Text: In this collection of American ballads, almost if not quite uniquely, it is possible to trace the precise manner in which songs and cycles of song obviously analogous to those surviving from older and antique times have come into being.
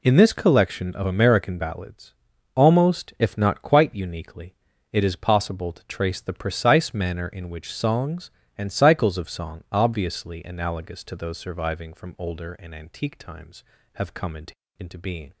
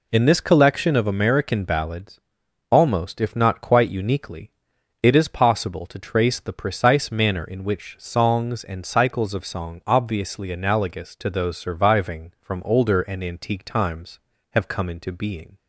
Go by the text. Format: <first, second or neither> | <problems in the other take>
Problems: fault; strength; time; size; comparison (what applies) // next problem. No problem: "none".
second | says "into" twice; at 14.7 s